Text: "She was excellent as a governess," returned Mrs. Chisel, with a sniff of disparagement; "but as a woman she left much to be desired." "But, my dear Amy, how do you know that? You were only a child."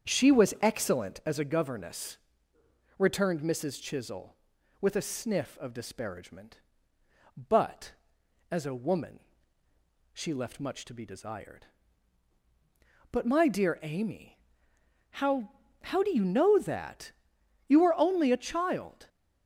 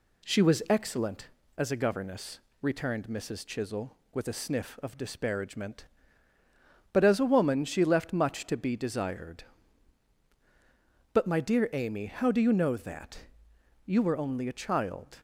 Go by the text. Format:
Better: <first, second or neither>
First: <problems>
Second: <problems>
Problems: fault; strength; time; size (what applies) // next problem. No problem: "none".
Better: second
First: starts louder than the rest; strong; until 1.1 s; 8 dB // pauses between "woman" and "she"; noticeable; at 9.1 s; 0.96 s long // says "how" twice; at 15.8 s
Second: none